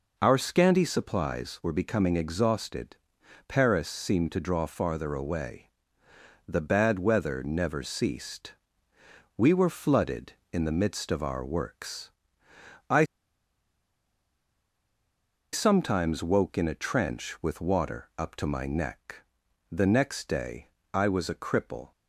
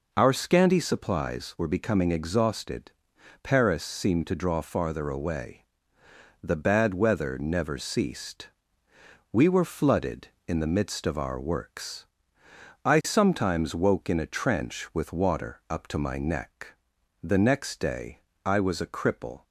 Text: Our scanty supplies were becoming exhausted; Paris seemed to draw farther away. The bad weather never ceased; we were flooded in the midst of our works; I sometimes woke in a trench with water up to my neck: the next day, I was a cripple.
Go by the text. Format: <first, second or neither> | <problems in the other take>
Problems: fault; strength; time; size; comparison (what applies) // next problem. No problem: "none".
second | pauses between "I" and "sometimes"; strong; at 13.0 s; 2.4 s long